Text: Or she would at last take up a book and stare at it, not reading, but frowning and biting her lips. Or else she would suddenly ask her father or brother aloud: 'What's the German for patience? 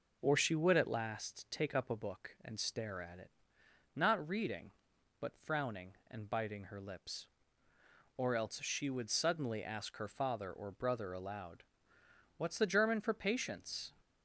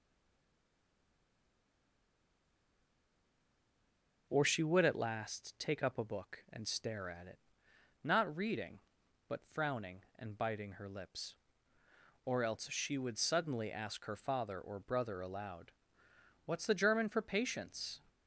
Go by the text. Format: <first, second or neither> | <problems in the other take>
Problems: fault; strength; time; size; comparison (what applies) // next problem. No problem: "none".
first | stays silent before the first word; strong; until 4.2 s; 4.2 s long